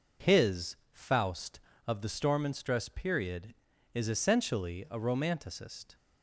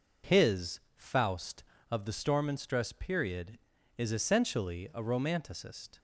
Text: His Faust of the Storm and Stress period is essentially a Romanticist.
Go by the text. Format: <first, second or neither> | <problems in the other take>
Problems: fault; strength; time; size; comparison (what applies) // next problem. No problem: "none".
neither | pauses between "His" and "Faust"; slight; the same in both